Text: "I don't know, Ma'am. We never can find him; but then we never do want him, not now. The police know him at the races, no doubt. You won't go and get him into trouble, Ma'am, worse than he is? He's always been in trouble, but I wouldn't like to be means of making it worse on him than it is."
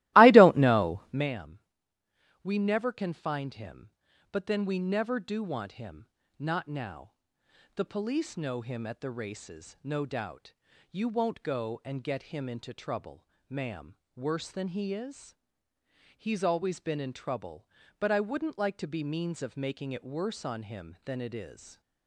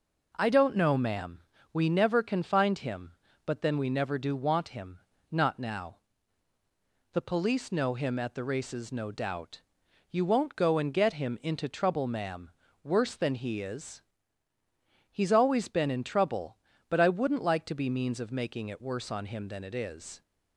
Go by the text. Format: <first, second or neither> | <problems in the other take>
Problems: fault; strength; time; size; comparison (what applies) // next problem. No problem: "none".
second | starts louder than the rest; strong; until 1.3 s; 17.5 dB // stays silent after the last word; slight; from 21.5 s on; 0.5 s long